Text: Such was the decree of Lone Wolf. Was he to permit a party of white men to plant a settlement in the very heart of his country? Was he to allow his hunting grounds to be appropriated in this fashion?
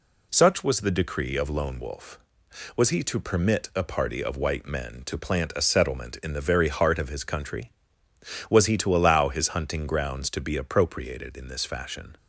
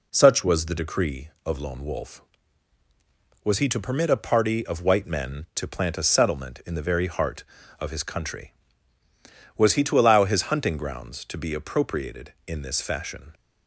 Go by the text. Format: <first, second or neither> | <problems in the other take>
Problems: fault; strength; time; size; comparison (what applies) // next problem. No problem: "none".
neither | none